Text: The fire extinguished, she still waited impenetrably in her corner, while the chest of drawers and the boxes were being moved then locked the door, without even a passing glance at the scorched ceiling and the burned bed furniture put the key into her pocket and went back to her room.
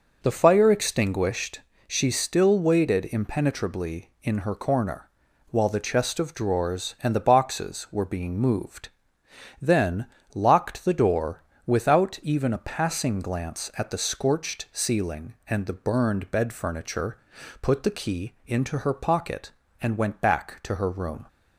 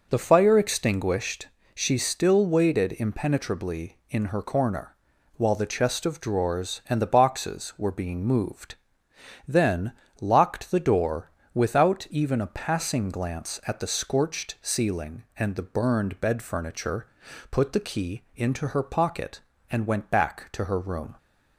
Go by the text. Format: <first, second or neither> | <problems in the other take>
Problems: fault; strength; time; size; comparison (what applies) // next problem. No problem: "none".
neither | pauses between "moved" and "then"; noticeable; the same in both // pauses between "then" and "locked"; slight; the same in both // pauses between "furniture" and "put"; the same in both